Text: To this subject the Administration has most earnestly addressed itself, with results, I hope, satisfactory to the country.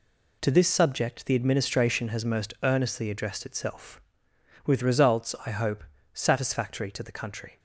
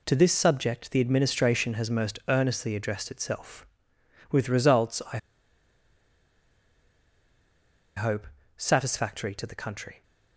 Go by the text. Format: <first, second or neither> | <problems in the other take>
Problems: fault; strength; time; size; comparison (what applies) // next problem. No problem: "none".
first | pauses between "I" and "hope"; strong; at 5.1 s; 2.7 s long